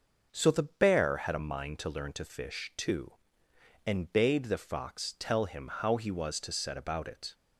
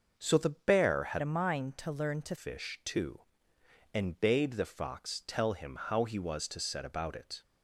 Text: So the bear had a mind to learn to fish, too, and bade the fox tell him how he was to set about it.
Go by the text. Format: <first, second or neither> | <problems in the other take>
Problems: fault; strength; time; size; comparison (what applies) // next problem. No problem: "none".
first | starts louder than the rest; noticeable; until 1.1 s; 6 dB // changes voice from "a" to "to"; from 1.1 to 2.3 s; 1.2 s long